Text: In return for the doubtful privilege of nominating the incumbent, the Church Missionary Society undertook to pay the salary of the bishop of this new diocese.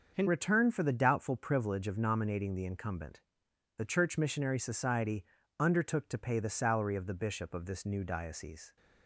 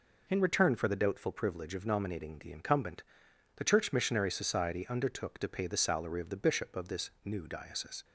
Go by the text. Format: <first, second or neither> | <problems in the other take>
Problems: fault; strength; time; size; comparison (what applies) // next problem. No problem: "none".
second | starts louder than the rest; until 1.1 s; 6.5 dB // changes voice at "return"; from 0.2 s on; 8.5 s long // pauses between "Society" and "undertook"; slight; at 5.2 s; 0.32 s long